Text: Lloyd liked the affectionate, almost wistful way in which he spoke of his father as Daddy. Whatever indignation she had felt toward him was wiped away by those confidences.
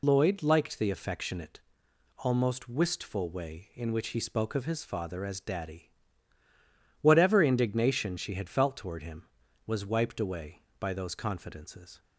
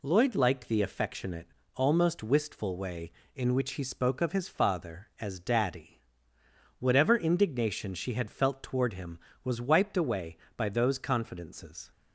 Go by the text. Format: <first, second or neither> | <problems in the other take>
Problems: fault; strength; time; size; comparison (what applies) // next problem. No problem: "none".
second | loses the start of "Lloyd"; at 0.0 s; 55 ms